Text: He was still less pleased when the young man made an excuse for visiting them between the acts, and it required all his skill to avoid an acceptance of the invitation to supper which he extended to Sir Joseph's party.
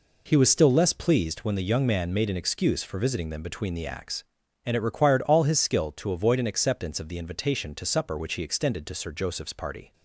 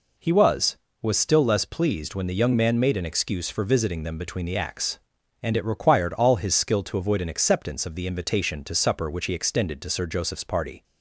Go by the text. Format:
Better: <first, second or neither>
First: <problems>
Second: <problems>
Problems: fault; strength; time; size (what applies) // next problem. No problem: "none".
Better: first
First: none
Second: says "was" twice; at 1.0 s